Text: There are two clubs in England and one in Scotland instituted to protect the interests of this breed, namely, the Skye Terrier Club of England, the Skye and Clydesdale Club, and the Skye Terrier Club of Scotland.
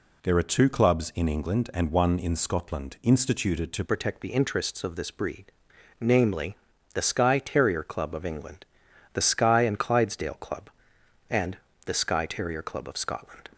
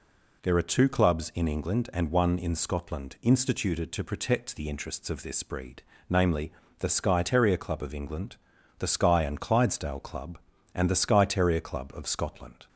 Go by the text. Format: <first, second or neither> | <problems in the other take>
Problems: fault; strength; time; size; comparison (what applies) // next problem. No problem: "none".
second | changes voice at "protect"; from 3.8 s on; 9.6 s long // pauses between "and" and "the"; slight; at 11.5 s; 0.28 s long